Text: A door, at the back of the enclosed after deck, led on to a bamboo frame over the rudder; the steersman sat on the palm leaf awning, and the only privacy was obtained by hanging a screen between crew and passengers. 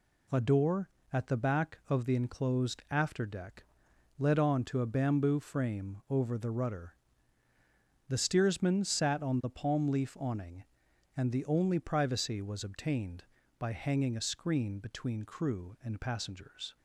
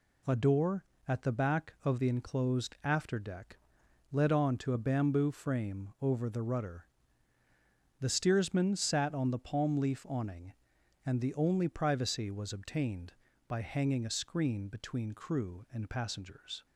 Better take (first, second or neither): neither